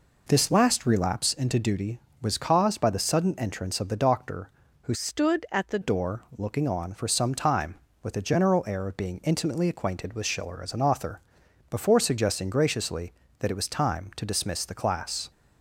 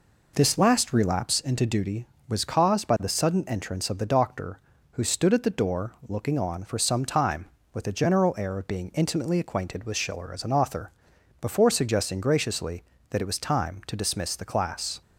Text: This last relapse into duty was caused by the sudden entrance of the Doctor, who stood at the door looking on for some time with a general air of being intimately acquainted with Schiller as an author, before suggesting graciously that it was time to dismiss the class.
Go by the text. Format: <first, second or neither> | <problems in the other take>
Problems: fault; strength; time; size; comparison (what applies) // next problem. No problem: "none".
second | changes voice from "stood" to "the"; from 4.9 to 5.7 s; 0.8 s long